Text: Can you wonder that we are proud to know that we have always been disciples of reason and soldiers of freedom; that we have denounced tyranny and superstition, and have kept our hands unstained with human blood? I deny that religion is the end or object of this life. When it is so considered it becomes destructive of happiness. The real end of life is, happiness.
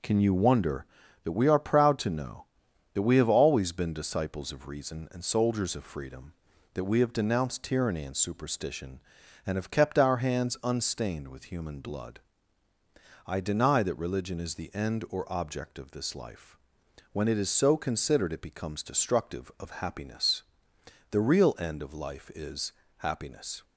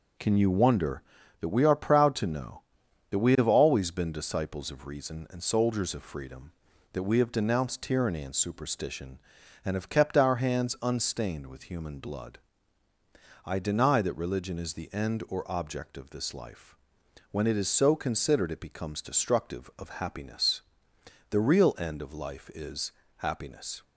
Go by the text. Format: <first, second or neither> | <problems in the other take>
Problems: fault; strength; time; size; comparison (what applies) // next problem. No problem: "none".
neither | none